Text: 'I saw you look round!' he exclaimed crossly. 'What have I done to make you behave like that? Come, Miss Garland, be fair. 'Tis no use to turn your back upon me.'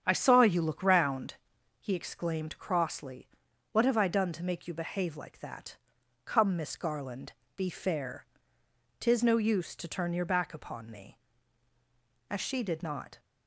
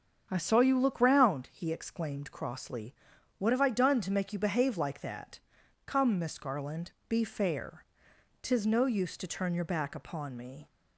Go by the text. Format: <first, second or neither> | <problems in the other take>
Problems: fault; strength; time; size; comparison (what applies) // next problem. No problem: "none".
second | starts louder than the rest; strong; until 1.0 s; 8 dB; also in the second // goes on to say "As she did not"; noticeable; from 12.2 s on; 0.90 s long